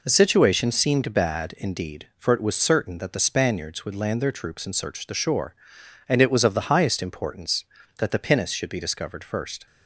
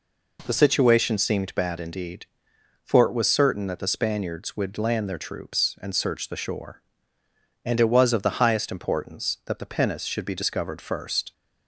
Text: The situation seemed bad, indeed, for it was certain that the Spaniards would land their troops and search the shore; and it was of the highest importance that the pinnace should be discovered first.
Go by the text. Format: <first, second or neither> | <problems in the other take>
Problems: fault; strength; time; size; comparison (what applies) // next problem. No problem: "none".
neither | none